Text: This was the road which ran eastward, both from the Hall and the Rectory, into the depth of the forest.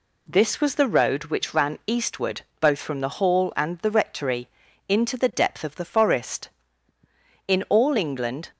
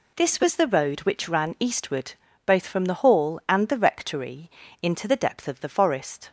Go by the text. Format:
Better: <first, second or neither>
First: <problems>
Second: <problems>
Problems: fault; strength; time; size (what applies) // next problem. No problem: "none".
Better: second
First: goes on to say "In all England"; noticeable; from 7.4 s on; 1.0 s long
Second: none